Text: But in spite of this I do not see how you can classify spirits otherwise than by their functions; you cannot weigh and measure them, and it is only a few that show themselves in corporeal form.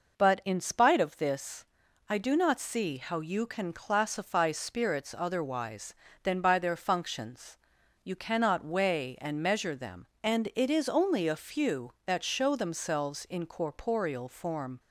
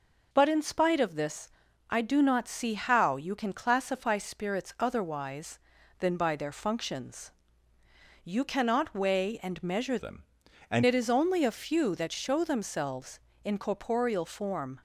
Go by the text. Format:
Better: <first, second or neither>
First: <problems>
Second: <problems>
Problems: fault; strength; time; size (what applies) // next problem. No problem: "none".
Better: first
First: pauses between "this" and "I"; at 1.6 s; 0.44 s long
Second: pauses between "this" and "I"; at 1.4 s; 0.40 s long // changes voice from "them" to "and"; from 9.9 to 10.8 s; 0.9 s long